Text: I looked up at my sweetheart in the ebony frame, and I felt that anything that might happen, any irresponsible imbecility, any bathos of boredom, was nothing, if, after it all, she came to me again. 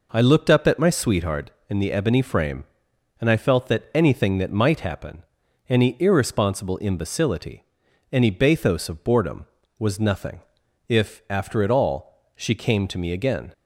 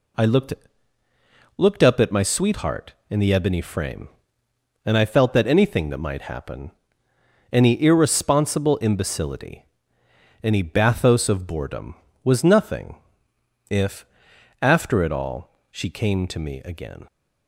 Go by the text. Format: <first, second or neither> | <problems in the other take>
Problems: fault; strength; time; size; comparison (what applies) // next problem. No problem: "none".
first | says "looked" twice; at 1.5 s